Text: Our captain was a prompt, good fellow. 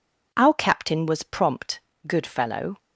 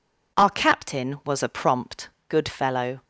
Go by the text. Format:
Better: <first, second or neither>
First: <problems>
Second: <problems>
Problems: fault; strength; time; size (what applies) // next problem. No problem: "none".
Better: second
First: skips "a"; at 1.2 s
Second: none